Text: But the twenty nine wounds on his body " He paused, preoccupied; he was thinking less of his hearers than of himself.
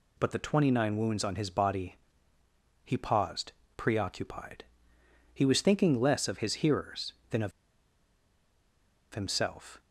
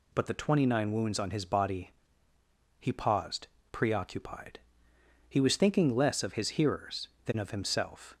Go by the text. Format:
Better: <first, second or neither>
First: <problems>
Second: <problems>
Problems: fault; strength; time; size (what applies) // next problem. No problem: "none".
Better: second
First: pauses between "of" and "himself"; strong; at 7.5 s; 1.6 s long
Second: none